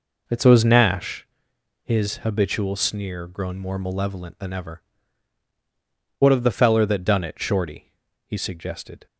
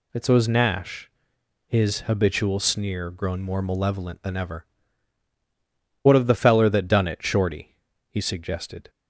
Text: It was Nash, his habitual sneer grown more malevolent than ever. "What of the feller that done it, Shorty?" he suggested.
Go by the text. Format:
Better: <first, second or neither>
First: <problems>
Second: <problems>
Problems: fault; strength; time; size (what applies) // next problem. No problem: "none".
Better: second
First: starts louder than the rest; noticeable; until 1.3 s; 5 dB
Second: none